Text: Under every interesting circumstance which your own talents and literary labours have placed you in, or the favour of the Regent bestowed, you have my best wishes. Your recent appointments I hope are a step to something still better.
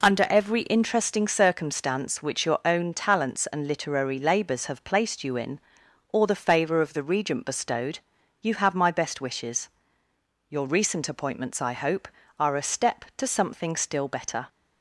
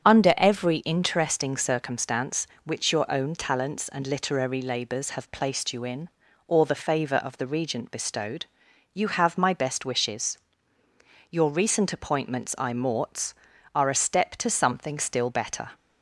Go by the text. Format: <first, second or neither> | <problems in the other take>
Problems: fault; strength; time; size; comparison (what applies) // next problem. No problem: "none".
first | starts louder than the rest; strong; until 1.0 s; 8.5 dB // says "morts" for "hope"; at 12.7 s